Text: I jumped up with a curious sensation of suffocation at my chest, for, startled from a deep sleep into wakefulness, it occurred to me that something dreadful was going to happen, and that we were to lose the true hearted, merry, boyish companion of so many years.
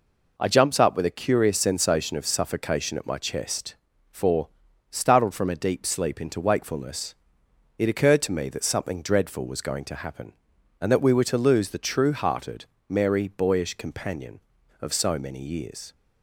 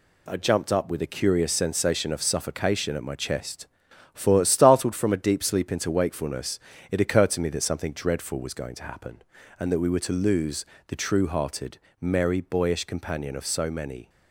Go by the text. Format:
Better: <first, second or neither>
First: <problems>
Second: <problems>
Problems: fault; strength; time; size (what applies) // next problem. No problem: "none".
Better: first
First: none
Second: pauses between "lose" and "the"; slight; at 10.6 s; 0.24 s long // stops before "years"; at 14.0 s